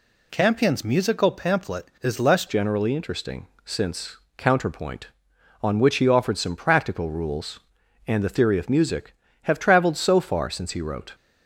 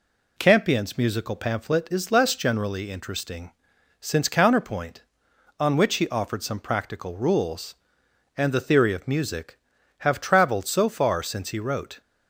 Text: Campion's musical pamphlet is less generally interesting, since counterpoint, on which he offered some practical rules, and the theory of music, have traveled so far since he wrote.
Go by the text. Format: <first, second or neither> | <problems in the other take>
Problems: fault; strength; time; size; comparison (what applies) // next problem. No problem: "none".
second | changes voice at "generally"; from 2.4 s on; 8.7 s long // pauses between "since" and "counterpoint"; slight; at 4.1 s; 0.20 s long